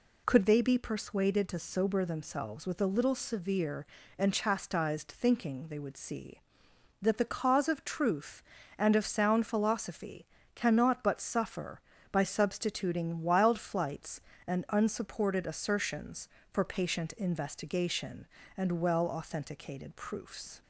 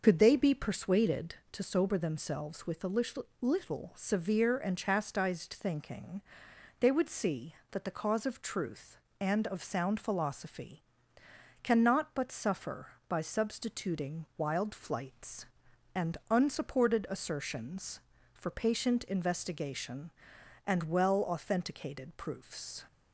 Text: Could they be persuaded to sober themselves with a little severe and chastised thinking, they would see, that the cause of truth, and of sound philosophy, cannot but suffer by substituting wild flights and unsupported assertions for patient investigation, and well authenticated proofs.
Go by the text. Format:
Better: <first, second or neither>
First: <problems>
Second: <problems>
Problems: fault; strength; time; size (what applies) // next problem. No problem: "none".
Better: first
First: none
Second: says "little" twice; at 3.4 s